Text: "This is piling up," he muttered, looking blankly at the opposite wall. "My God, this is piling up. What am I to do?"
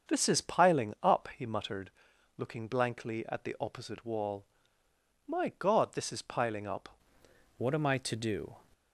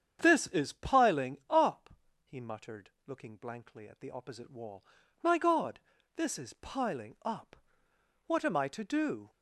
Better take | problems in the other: second | starts louder than the rest; until 1.1 s; 7 dB; strong in the second // changes voice at "What"; from 7.5 s on; 1.0 s long

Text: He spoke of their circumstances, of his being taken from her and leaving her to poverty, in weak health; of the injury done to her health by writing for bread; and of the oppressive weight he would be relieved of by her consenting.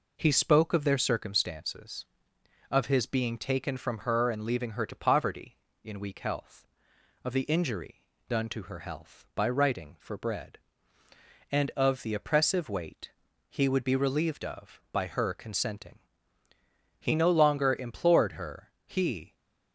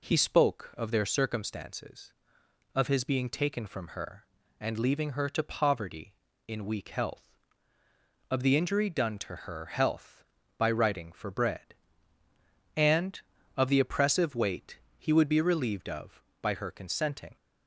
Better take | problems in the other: second | pauses between "injury" and "done"; slight; at 8.0 s; 0.26 s long // pauses between "weight" and "he"; at 13.1 s; 0.40 s long; slight in the second // goes on to say "He no longer implored her he"; strong; from 16.9 s on; 2.3 s long

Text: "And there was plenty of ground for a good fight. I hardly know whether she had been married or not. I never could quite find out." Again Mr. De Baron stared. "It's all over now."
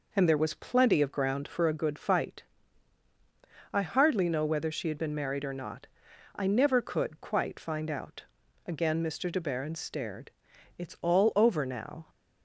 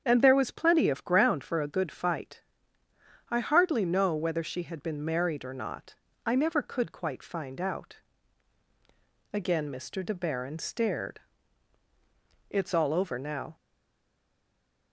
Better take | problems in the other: first | starts louder than the rest; strong; until 1.0 s; 7.5 dB // stays silent after the last word; noticeable; from 13.5 s on; 1.4 s long

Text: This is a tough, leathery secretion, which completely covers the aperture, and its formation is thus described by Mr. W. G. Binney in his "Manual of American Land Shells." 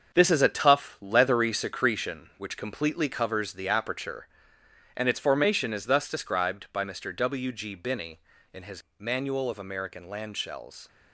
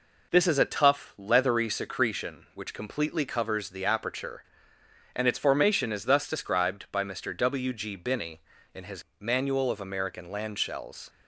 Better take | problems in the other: second | gets quieter; strong; throughout; 7.5 dB // pauses between "his" and "Manual"; slight; at 8.8 s; 0.16 s long; slight in the second

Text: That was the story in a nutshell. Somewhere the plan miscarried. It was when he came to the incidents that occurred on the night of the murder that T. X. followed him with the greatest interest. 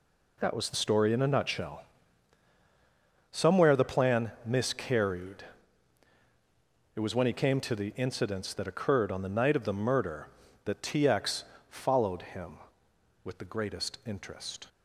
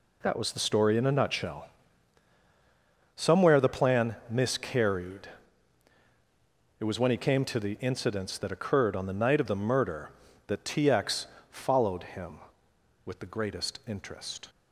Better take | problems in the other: neither | pauses between "X" and "followed"; slight; the same in both

